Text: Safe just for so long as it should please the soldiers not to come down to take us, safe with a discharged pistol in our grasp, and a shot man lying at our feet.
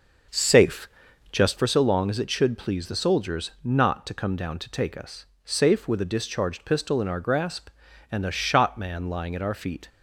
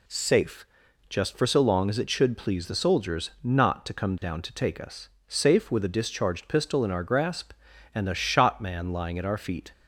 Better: second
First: starts louder than the rest; noticeable; until 1.6 s; 6 dB // pauses between "Safe" and "just"; at 0.8 s; 0.42 s long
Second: pauses between "Safe" and "just"; at 0.6 s; 0.42 s long

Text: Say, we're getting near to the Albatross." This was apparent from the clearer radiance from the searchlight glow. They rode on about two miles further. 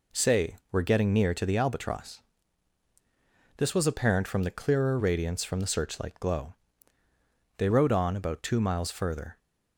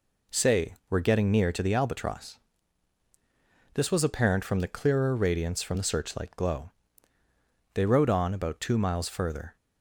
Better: neither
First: none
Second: none

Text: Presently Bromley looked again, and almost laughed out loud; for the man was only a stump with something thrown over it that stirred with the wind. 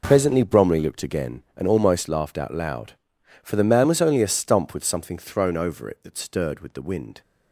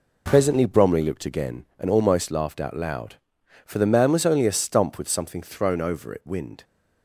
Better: first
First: none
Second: skips "that stirred with the"; at 6.2 s

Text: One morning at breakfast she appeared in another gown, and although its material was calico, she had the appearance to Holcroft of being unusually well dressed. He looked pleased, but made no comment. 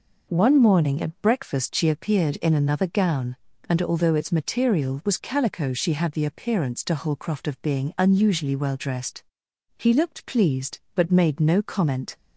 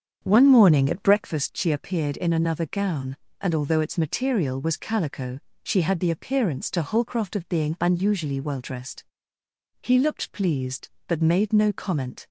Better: first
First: none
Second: starts louder than the rest; strong; until 1.4 s; 7.5 dB

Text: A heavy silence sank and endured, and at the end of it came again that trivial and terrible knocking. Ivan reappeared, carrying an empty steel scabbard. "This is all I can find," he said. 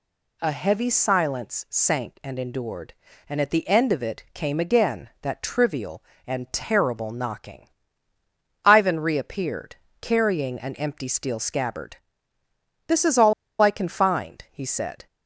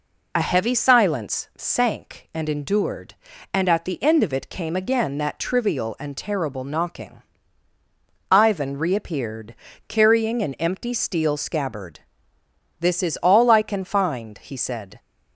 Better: second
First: pauses between "all" and "I"; slight; at 13.3 s; 0.29 s long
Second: none

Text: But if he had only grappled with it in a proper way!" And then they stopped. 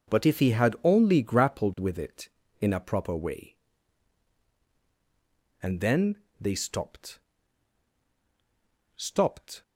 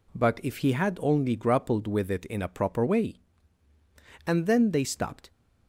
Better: second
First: pauses between "then" and "they"; slight; at 6.1 s; 0.22 s long // says "stopped" twice; at 8.9 s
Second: none

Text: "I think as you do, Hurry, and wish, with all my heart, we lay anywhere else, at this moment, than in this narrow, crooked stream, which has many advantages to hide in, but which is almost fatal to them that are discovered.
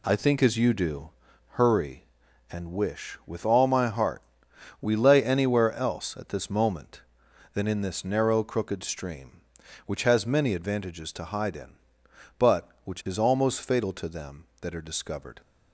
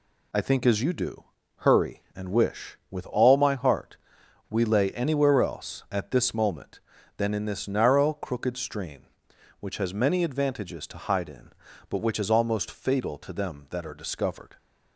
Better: neither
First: none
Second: none

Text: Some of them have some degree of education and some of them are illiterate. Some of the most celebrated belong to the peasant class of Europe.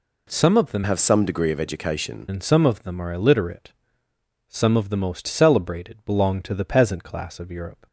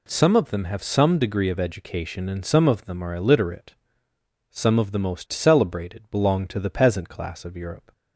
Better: second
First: changes voice from "have" to "education"; from 0.8 to 2.2 s; 1.4 s long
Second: none

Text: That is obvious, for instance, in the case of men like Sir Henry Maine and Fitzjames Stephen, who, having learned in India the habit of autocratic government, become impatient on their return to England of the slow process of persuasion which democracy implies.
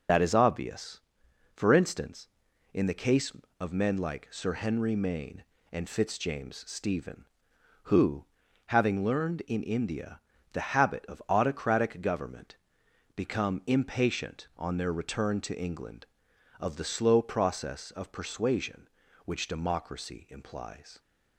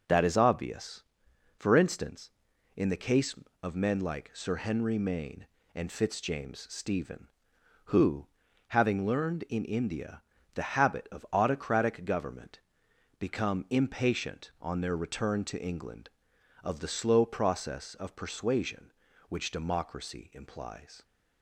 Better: second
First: loses the start of "That"; at 0.0 s; 55 ms // pauses between "India" and "the"; slight; at 10.1 s; 0.34 s long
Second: pauses between "India" and "the"; slight; at 10.2 s; 0.34 s long

